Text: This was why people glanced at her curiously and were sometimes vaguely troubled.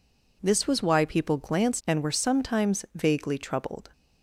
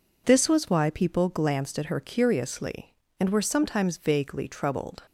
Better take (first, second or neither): second